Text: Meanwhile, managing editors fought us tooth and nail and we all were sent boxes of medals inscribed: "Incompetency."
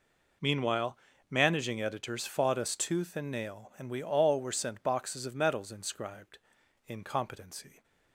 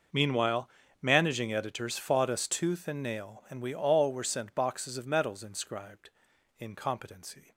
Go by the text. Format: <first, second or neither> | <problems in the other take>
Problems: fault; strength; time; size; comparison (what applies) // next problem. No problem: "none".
first | gets quieter; strong; throughout; 20 dB